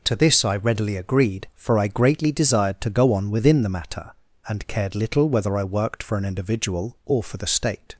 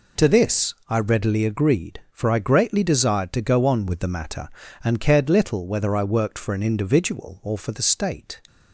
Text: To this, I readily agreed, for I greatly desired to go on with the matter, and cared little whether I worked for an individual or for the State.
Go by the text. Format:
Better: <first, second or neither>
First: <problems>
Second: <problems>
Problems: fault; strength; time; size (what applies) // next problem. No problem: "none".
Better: second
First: says "within" for "with"; at 3.2 s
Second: none